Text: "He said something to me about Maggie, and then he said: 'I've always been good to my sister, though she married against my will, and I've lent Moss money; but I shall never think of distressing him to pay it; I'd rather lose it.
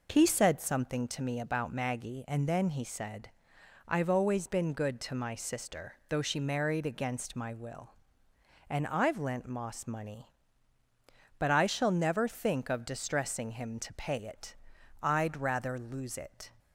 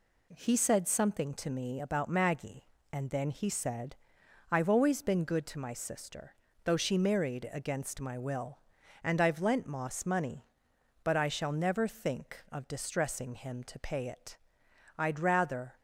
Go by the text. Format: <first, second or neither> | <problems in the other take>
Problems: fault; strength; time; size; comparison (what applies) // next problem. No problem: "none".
first | stops before "lose it"; at 15.7 s